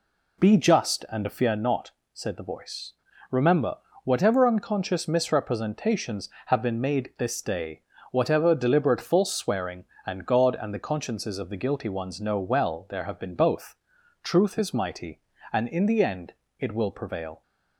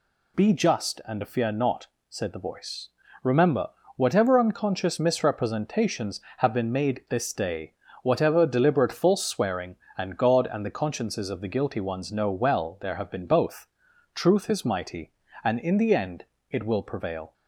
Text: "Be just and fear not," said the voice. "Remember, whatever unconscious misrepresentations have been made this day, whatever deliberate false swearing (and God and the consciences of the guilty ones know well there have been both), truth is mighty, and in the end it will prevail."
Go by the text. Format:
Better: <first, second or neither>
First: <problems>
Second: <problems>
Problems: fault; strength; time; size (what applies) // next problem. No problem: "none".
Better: second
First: starts louder than the rest; slight; until 1.7 s; 3 dB // pauses between "end" and "it"; slight; at 16.3 s; 0.24 s long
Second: pauses between "end" and "it"; slight; at 16.2 s; 0.24 s long